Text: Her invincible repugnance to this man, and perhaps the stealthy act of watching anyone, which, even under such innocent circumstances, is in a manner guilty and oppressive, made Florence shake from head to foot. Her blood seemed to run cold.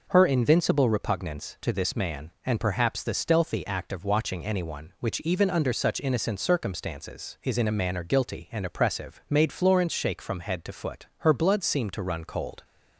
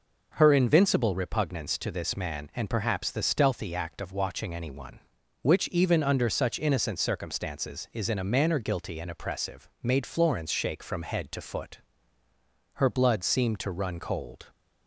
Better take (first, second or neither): neither